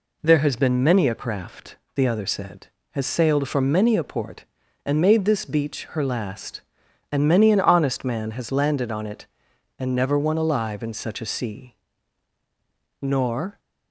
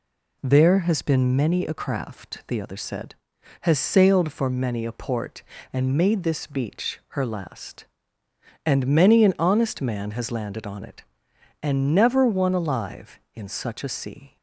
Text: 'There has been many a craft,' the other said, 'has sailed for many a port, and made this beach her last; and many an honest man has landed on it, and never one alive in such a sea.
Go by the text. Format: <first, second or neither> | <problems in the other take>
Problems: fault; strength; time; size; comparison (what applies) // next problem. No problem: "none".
second | goes on to say "Nor"; from 12.9 s on; 0.60 s long